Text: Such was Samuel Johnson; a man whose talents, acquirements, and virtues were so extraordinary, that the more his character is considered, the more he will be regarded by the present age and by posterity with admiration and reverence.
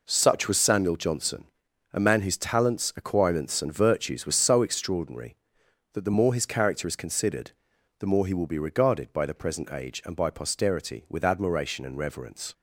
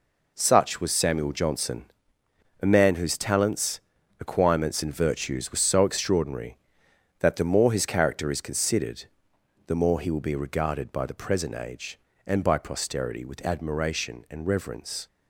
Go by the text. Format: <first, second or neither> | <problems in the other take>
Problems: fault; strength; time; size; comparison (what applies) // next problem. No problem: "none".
neither | none